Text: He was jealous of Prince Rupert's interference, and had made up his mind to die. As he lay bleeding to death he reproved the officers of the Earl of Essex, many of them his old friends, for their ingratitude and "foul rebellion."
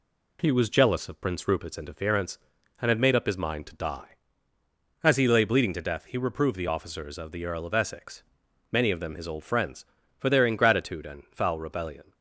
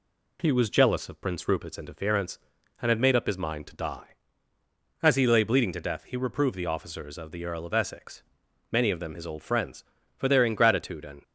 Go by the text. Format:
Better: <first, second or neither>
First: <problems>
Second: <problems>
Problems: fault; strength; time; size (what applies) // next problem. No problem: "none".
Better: first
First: none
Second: stops before "foul rebellion"; at 11.2 s